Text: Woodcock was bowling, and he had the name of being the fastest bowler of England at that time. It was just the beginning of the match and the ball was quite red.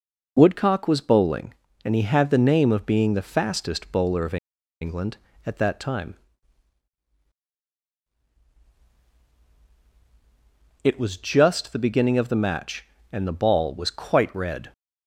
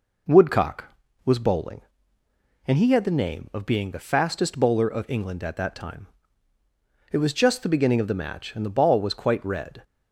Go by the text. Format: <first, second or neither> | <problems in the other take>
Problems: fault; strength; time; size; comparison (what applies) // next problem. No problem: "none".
second | pauses between "of" and "England"; at 4.3 s; 0.45 s long